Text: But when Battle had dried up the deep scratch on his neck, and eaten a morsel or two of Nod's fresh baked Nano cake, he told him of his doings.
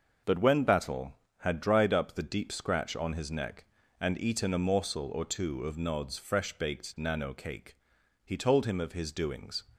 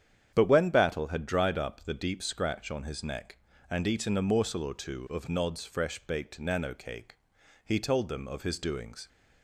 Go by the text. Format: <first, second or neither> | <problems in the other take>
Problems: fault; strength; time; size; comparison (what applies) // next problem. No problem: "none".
first | starts louder than the rest; strong; until 1.3 s; 9 dB; noticeable in the first // says "them" for "him"; at 8.0 s